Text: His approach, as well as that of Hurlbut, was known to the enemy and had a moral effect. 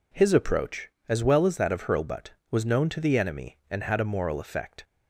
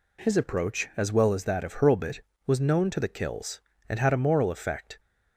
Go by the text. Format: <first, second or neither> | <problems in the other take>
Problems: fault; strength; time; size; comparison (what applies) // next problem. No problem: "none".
first | says "kills" for "enemy"; at 3.0 s